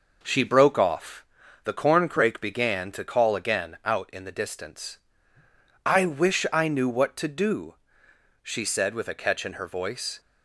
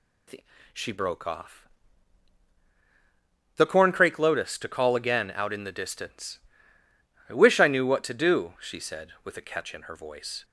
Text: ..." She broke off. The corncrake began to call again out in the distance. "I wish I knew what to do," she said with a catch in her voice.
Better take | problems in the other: first | says "lotus" for "began"; at 4.1 s

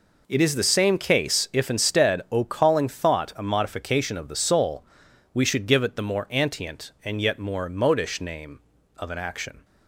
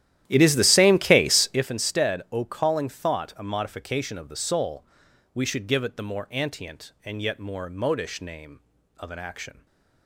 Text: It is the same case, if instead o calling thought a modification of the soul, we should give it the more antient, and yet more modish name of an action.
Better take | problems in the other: first | starts louder than the rest; strong; until 1.6 s; 12.5 dB

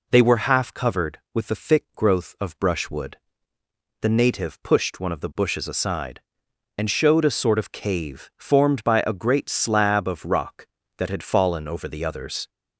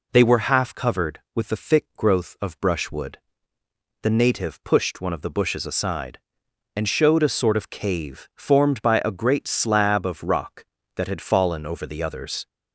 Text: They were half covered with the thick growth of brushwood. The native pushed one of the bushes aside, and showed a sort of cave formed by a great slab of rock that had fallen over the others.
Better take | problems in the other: neither | none

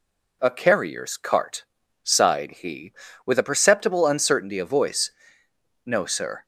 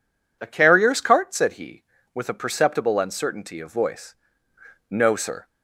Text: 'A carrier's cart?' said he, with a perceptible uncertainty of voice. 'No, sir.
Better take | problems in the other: second | says "sighed" for "said"; at 2.0 s

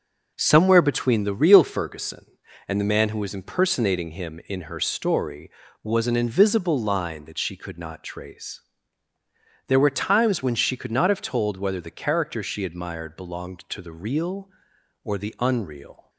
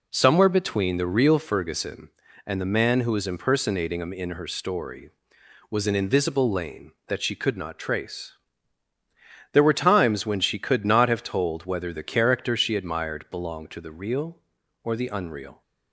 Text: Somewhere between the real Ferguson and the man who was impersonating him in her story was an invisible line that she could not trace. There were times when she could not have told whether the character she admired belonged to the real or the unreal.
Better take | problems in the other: first | says "lane" for "line"; at 6.5 s

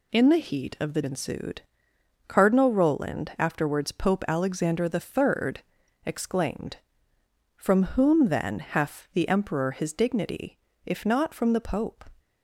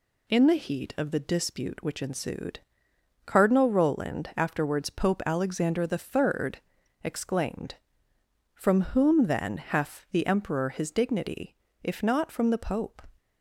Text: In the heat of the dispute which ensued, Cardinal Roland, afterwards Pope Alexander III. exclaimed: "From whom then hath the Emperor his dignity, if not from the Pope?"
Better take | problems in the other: second | skips "dispute which"; at 1.0 s // pauses between "From" and "whom"; slight; at 7.8 s; 0.16 s long; slight in the second

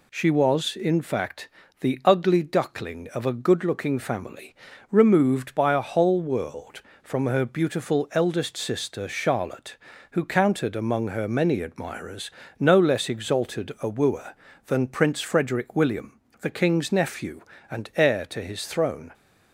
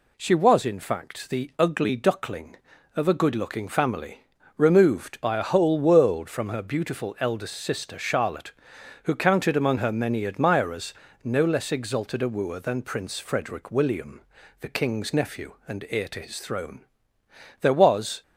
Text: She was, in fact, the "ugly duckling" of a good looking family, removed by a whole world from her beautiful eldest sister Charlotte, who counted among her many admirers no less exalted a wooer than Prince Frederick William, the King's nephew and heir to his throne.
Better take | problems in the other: first | pauses between "admirers" and "no"; slight; at 10.9 s; 0.30 s long; slight in the first // goes on to say "There was"; noticeable; from 17.5 s on; 0.62 s long

